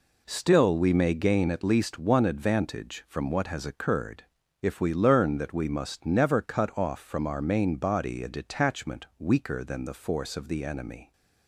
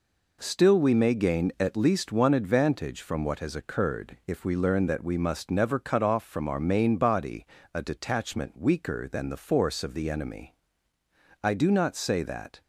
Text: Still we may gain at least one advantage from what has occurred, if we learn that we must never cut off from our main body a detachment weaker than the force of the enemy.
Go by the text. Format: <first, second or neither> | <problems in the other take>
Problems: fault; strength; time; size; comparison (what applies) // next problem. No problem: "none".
first | pauses between "body" and "a"; slight; at 7.4 s; 0.28 s long // goes on to say "I do not say that"; noticeable; from 11.4 s on; 1.1 s long